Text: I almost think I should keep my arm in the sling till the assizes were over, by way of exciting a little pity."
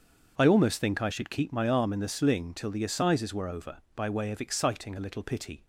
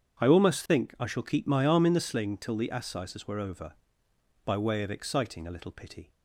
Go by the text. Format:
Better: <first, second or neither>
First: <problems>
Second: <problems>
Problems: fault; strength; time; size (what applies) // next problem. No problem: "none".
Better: first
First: starts louder than the rest; until 1.3 s; 6.5 dB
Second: starts louder than the rest; strong; until 1.3 s; 7.5 dB // says "shall" for "should"; at 1.0 s